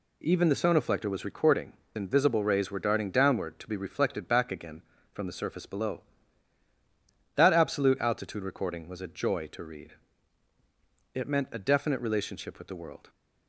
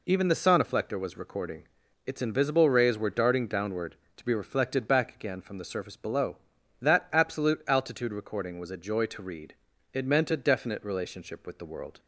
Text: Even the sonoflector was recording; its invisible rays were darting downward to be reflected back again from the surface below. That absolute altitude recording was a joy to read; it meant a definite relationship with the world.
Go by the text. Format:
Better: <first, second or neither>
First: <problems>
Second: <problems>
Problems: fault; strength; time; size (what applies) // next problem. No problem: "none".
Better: second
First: skips "its"; at 1.8 s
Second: none